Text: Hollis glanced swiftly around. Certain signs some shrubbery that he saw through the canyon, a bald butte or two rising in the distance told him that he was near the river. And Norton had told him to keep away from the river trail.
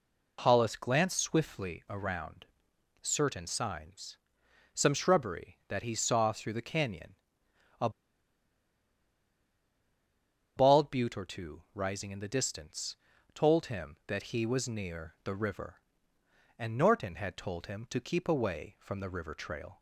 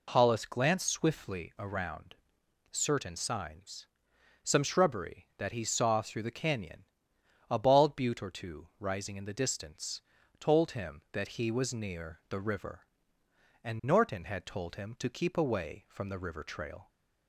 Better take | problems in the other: second | pauses between "signs" and "some"; noticeable; at 4.1 s; 0.58 s long; noticeable in the second // pauses between "a" and "bald"; strong; at 7.8 s; 2.6 s long // pauses between "distance" and "told"; at 12.9 s; 0.38 s long; also in the second

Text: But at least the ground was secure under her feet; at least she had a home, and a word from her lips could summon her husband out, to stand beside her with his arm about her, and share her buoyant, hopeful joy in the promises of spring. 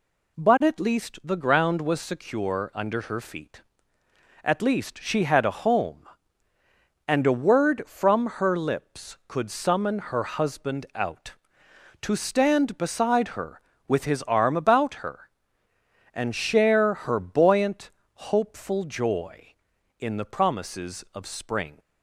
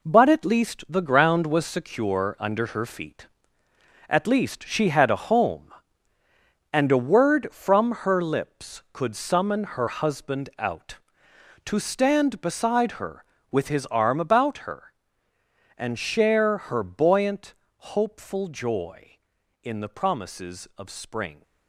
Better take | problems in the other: first | gets quieter; strong; throughout; 7.5 dB

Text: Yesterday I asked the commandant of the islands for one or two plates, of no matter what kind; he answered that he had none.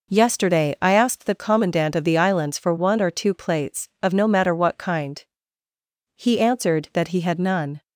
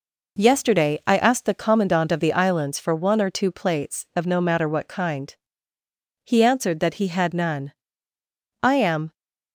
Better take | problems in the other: first | goes on to say "I am"; from 8.6 s on; 0.52 s long

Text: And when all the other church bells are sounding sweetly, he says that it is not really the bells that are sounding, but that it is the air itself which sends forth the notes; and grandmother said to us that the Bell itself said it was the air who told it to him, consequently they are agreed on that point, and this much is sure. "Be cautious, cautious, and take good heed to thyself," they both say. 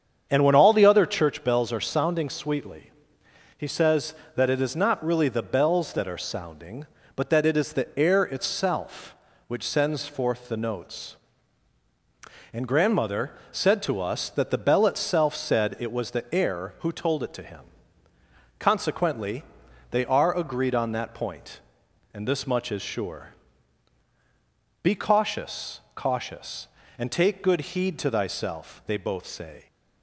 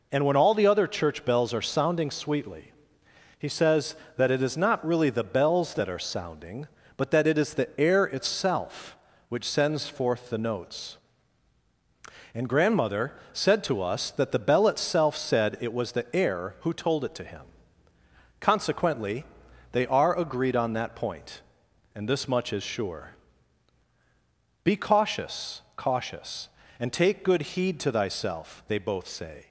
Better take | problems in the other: second | starts louder than the rest; strong; until 1.3 s; 8 dB // pauses between "grandmother" and "said"; slight; at 13.3 s; 0.20 s long; slight in the second // pauses between "consequently" and "they"; noticeable; at 19.4 s; 0.48 s long; noticeable in the second

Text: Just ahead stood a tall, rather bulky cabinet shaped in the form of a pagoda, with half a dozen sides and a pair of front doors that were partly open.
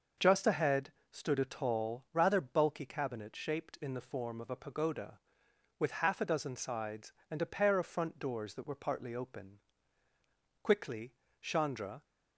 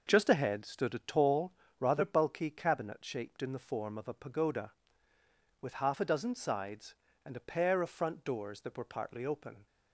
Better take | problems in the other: second | starts louder than the rest; noticeable; until 1.4 s; 6 dB // pauses between "ahead" and "stood"; slight; at 0.9 s; 0.22 s long // goes on to say "Quickly Chandra"; from 10.6 s on; 1.4 s long

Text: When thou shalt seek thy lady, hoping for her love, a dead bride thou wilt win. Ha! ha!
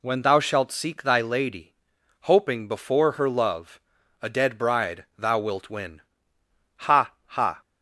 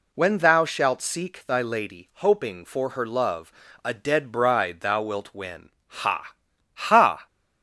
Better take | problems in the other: second | says "before" for "for"; at 2.6 s

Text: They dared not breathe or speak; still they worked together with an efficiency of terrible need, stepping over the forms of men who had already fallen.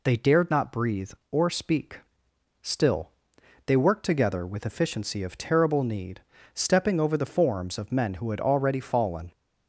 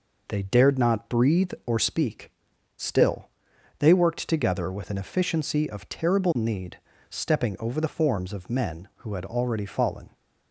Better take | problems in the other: second | pauses between "still" and "they"; noticeable; at 3.0 s; 0.56 s long; noticeable in the second // skips "an"; at 4.6 s

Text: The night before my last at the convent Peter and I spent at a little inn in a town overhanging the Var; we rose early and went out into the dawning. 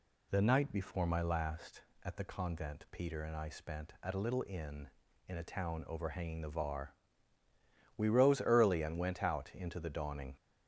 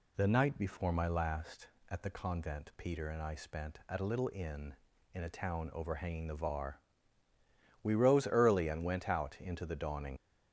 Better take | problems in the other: first | leaves "dawning" unfinished; at 10.1 s; 50 ms

